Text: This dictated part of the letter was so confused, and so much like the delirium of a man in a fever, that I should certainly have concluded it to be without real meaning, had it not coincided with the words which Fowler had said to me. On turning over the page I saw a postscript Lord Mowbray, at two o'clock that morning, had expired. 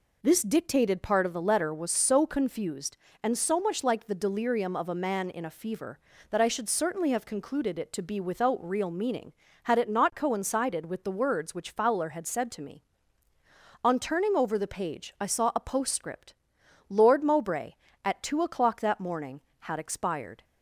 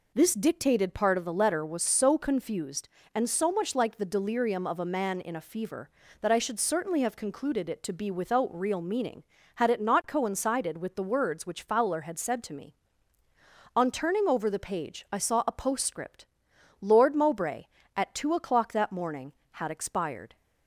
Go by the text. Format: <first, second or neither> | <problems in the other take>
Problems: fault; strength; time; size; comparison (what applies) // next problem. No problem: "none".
neither | pauses between "postscript" and "Lord"; noticeable; the same in both